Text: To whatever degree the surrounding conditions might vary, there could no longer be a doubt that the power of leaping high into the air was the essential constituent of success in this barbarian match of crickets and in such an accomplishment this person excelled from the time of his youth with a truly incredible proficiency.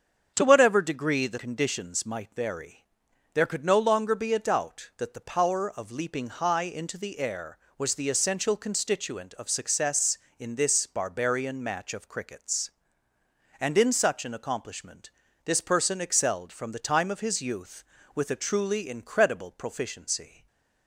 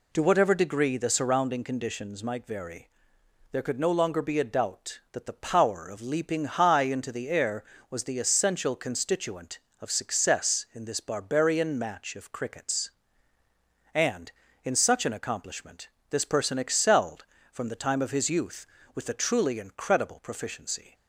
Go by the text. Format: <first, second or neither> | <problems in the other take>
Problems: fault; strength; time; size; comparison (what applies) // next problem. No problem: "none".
second | starts louder than the rest; strong; until 1.3 s; 7.5 dB // skips "surrounding"; at 1.3 s // pauses between "accomplishment" and "this"; slight; at 15.1 s; 0.34 s long; slight in the second // stays silent after the last word; slight; from 20.2 s on; 0.6 s long